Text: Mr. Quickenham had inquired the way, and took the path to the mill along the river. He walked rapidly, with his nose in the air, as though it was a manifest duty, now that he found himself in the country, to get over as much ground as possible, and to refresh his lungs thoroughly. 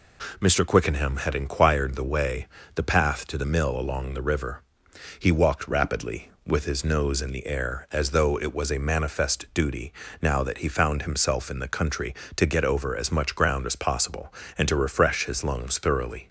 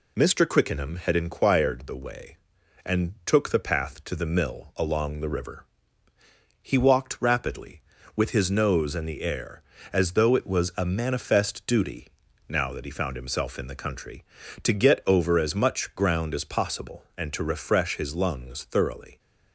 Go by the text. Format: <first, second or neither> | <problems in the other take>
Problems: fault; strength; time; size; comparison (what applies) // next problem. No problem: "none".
second | skips "and took"; at 2.6 s